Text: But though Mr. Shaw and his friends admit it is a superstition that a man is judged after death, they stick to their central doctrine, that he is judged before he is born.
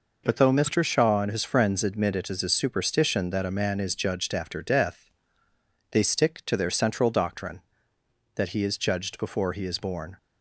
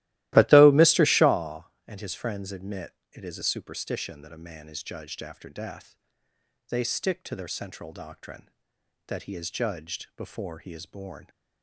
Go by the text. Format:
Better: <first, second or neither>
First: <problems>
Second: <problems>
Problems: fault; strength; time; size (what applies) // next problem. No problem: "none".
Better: first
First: none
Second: starts louder than the rest; strong; until 1.3 s; 16.5 dB // pauses between "admit" and "it"; slight; at 2.9 s; 0.18 s long